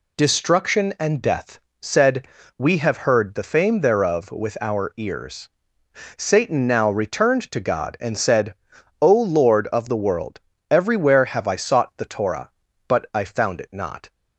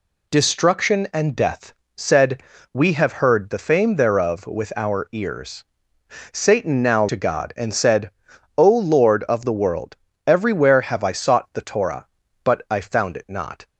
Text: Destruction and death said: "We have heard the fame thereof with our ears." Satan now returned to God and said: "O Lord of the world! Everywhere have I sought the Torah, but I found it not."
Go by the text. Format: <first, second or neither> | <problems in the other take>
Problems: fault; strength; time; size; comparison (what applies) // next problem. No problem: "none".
first | pauses between "death" and "said"; slight; at 1.7 s; 0.24 s long; slight in the first // skips "returned"; at 7.0 s